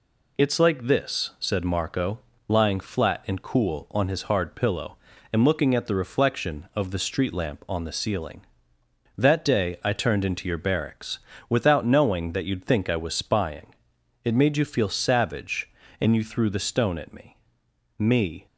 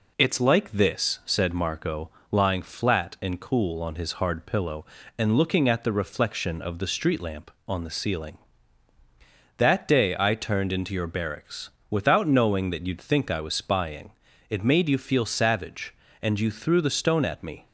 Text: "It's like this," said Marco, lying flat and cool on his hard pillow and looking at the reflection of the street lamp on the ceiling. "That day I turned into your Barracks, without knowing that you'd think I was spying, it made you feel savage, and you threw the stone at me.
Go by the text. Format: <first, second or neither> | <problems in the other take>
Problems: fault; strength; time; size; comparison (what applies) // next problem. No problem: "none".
second | says "me" twice; at 17.9 s